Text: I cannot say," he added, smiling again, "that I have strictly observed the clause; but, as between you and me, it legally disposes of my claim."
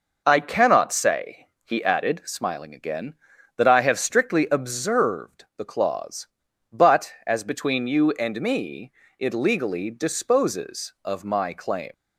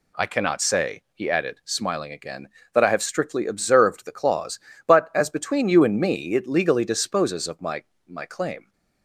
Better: first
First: none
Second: says "my" twice; at 8.0 s

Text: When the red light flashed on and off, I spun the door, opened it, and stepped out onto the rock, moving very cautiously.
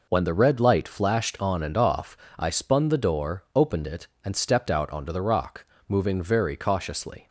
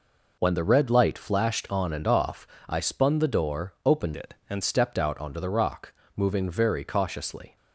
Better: first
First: none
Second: changes voice from "it" to "and"; from 4.1 to 4.6 s; 0.5 s long

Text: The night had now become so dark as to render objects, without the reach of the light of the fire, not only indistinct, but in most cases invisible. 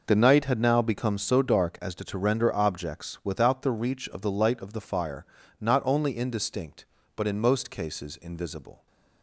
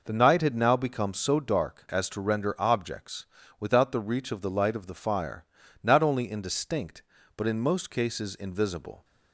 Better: second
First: says "to" twice; at 2.0 s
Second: none

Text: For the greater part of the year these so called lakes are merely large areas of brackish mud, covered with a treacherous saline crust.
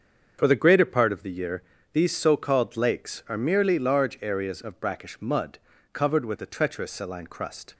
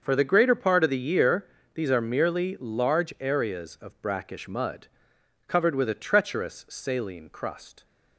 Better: first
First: starts louder than the rest; until 1.4 s; 7 dB // pauses between "year" and "these"; slight; at 1.6 s; 0.28 s long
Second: starts louder than the rest; until 1.0 s; 6.5 dB // pauses between "year" and "these"; slight; at 1.4 s; 0.28 s long // skips "so called lakes"; at 1.8 s

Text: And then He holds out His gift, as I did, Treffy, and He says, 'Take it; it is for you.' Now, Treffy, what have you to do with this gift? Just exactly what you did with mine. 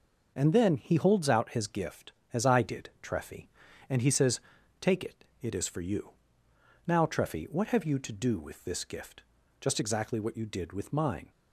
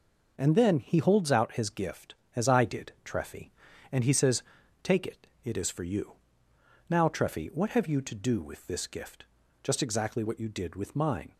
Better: neither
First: none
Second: none

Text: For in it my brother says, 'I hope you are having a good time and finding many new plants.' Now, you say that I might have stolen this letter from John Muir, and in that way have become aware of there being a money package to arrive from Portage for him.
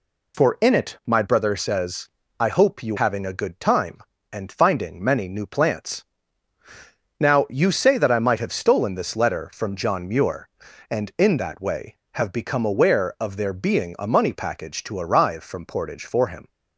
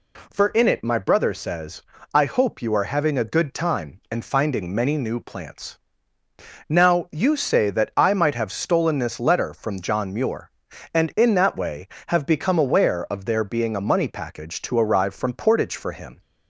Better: second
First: skips "are"; at 2.9 s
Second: none

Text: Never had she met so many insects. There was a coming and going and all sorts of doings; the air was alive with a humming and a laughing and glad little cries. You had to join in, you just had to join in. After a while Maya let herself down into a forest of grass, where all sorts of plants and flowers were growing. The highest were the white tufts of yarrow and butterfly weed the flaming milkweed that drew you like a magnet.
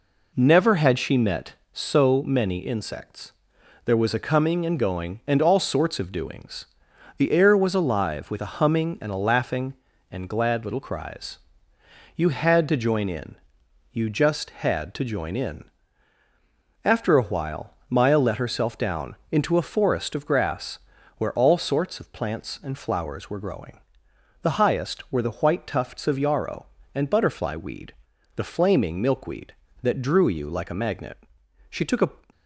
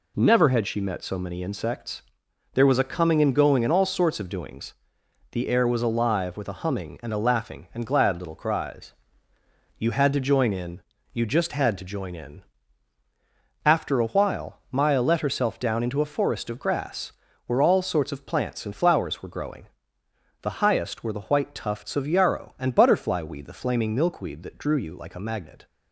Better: second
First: pauses between "while" and "Maya"; slight; at 17.7 s; 0.16 s long // pauses between "weed" and "the"; at 27.9 s; 0.42 s long // goes on to say "She took a"; from 31.6 s on; 0.54 s long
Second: none

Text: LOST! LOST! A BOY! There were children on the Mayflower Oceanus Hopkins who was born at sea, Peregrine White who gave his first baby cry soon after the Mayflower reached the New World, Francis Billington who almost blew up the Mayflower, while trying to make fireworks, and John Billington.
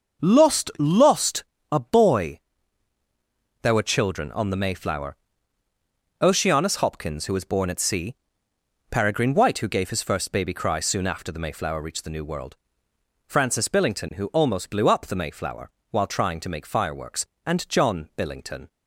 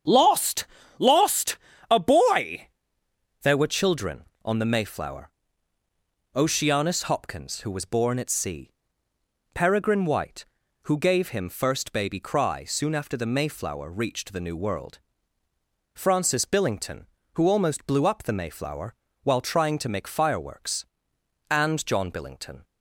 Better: first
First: starts louder than the rest; until 1.3 s; 6.5 dB // pauses between "Mayflower" and "Oceanus"; at 5.1 s; 1.0 s long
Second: starts louder than the rest; strong; until 1.4 s; 8 dB // pauses between "Mayflower" and "Oceanus"; at 5.3 s; 1.0 s long // says "him" for "his"; at 11.3 s

